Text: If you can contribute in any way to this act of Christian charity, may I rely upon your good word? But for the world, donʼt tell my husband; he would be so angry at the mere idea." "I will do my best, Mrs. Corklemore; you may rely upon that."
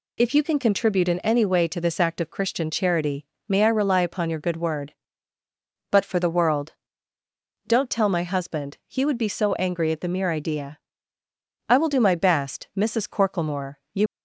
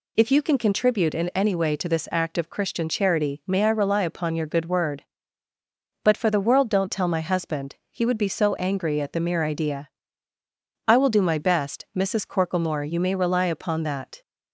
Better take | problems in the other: second | stops before "may rely upon that"; at 14.0 s

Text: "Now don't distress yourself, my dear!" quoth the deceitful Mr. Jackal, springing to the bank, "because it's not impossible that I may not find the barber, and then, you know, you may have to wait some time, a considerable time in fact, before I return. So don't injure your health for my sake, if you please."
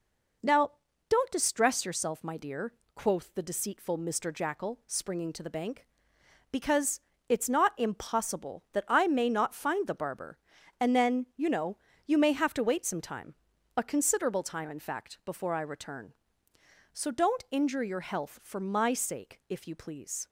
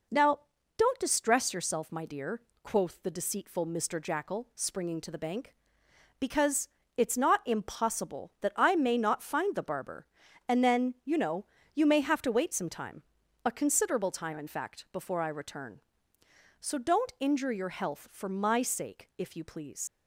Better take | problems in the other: first | pauses between "Now" and "don't"; slight; at 0.4 s; 0.36 s long; slight in the first // pauses between "because" and "it's"; slight; at 6.6 s; 0.28 s long; slight in the first // leaves "please" unfinished; at 19.8 s; 95 ms

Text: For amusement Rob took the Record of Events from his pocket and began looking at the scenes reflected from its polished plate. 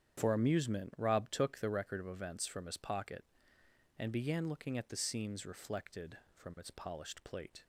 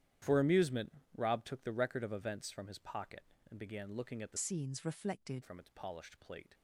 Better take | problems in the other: first | starts louder than the rest; strong; until 1.4 s; 11 dB; strong in the first // pauses between "amusement" and "Rob"; slight; at 0.9 s; 0.24 s long // changes voice from "scenes" to "reflected"; from 4.3 to 5.4 s; 1.1 s long

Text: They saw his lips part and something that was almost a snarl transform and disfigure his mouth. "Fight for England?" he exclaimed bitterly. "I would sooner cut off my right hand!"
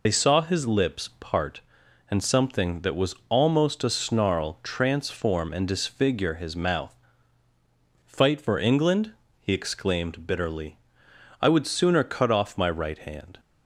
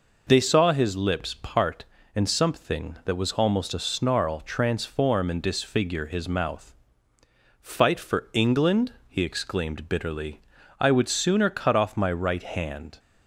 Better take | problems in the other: second | loses the start of "They"; at 0.0 s; 60 ms

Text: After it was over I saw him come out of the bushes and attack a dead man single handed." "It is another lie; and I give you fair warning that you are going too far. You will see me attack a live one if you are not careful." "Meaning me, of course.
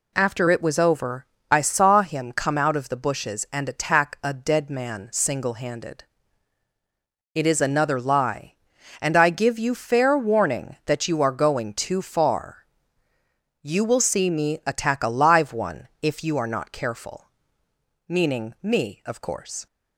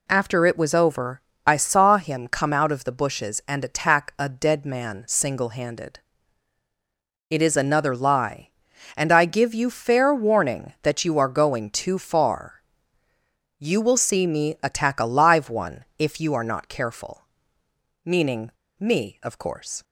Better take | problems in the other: first | pauses between "over" and "I"; slight; at 1.2 s; 0.24 s long; slight in the first // pauses between "one" and "if"; slight; at 15.8 s; 0.16 s long; slight in the first // pauses between "Meaning" and "me"; slight; at 18.5 s; 0.28 s long

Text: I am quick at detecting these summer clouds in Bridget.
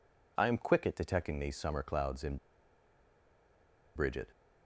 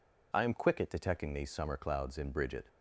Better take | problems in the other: second | pauses between "in" and "Bridget"; strong; at 2.3 s; 1.6 s long

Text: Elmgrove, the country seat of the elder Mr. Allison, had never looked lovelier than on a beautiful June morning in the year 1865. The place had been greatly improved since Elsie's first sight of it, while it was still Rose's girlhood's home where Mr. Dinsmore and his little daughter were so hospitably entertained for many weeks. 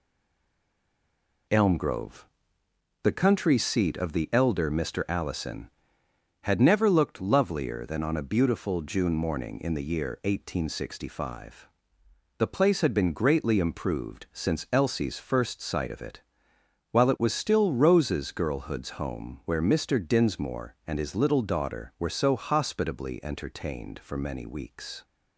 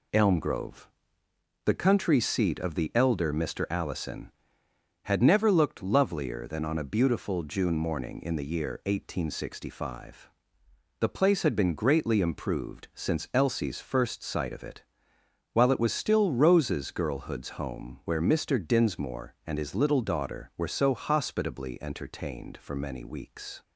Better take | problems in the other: second | stays silent before the first word; noticeable; until 1.4 s; 1.4 s long

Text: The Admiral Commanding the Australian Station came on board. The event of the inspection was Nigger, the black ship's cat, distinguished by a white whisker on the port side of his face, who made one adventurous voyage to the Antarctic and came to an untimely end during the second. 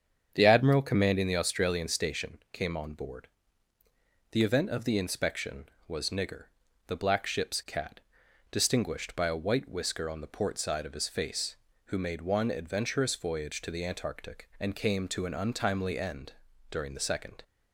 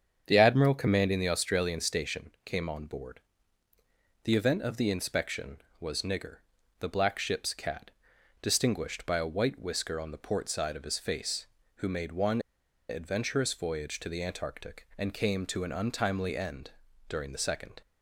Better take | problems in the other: first | starts louder than the rest; strong; until 1.2 s; 7.5 dB; strong in the first // pauses between "one" and "adventurous"; noticeable; at 12.3 s; 0.49 s long // pauses between "end" and "during"; at 16.7 s; 0.38 s long; also in the first

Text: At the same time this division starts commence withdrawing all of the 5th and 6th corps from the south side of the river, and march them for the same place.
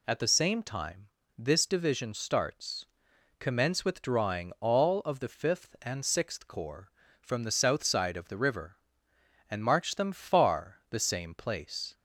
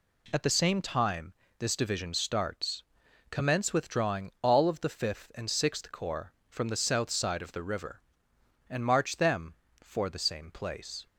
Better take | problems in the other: second | pauses between "time" and "this"; slight; at 1.0 s; 0.30 s long; slight in the second // pauses between "starts" and "commence"; noticeable; at 2.8 s; 0.52 s long; noticeable in the second // says "far" for "for"; at 10.1 s

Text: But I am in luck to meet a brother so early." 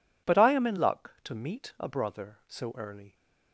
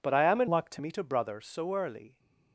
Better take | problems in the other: first | changes voice from "luck" to "to"; from 0.4 to 0.7 s; 0.3 s long

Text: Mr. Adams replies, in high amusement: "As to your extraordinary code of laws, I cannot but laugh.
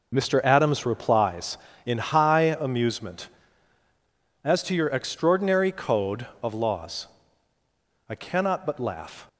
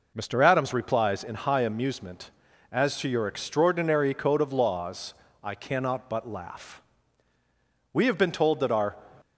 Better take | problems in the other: first | goes on to say "We have been told that our"; noticeable; from 7.9 s on; 1.0 s long

